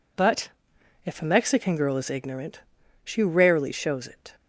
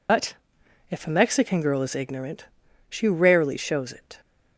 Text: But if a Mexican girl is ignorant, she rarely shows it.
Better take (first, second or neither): first